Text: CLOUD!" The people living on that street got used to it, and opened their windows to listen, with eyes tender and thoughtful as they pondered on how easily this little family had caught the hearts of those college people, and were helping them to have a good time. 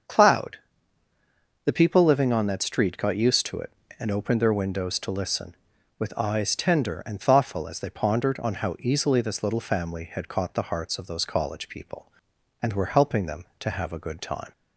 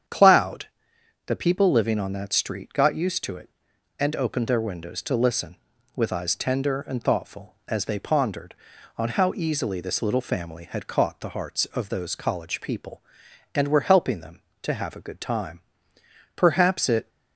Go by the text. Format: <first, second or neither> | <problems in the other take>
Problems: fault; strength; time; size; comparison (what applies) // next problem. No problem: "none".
first | starts louder than the rest; strong; until 1.6 s; 8.5 dB; also in the first // goes on to say "Perhaps it"; noticeable; from 16.3 s on; 0.72 s long